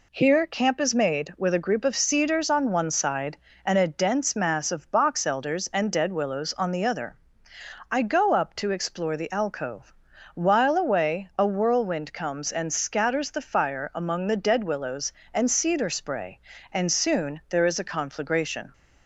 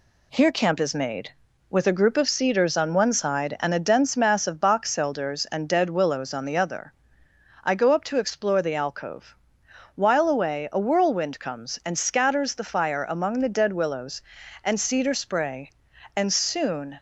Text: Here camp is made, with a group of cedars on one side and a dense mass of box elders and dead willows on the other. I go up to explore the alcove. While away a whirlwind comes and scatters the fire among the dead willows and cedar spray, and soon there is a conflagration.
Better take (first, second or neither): first